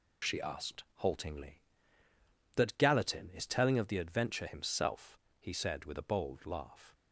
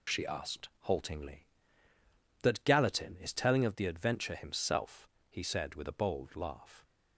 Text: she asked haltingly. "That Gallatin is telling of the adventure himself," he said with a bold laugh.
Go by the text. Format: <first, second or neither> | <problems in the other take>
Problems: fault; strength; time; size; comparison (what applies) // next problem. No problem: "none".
neither | none